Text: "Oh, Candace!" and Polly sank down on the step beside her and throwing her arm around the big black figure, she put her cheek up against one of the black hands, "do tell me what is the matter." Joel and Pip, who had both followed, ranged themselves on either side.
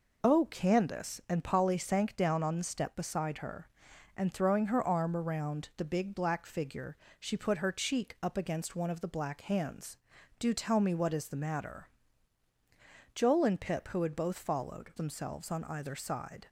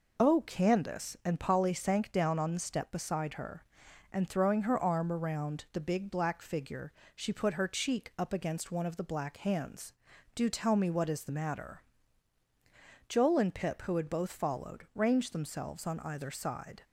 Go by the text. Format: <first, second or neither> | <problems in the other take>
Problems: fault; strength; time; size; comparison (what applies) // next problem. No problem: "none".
second | skips "ranged"; at 14.9 s